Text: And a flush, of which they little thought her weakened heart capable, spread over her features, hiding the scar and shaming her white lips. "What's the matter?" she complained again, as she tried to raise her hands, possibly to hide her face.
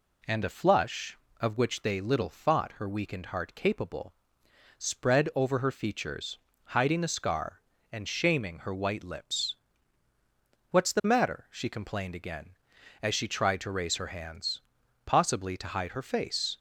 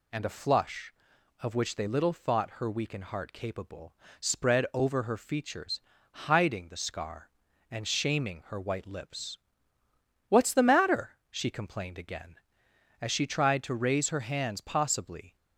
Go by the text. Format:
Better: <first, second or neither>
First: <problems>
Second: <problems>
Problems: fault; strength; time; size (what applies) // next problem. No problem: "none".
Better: first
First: none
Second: stops before "to hide her face"; at 15.3 s